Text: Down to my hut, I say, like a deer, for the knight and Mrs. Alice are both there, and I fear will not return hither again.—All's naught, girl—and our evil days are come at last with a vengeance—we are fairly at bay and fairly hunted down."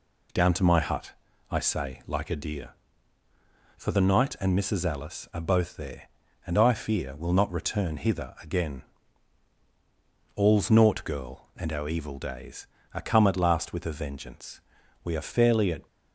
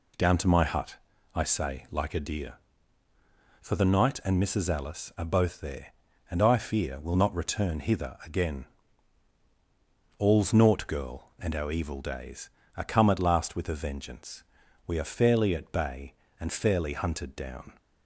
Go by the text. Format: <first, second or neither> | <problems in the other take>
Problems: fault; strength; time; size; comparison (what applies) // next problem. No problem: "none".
second | stops before "bay and fairly hunted down"; at 15.8 s